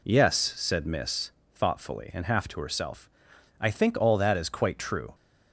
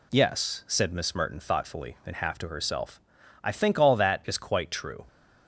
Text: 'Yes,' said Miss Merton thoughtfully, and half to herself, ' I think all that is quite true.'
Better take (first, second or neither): second